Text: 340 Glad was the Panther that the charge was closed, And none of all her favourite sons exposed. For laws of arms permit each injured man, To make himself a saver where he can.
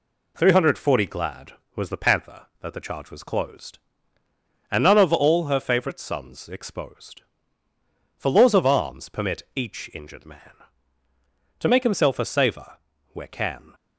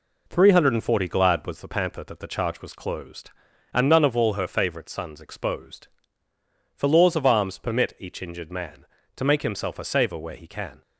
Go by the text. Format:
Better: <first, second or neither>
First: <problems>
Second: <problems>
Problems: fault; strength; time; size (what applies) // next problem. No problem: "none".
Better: second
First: pauses between "saver" and "where"; slight; at 12.7 s; 0.34 s long // skips "he"; at 13.2 s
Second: none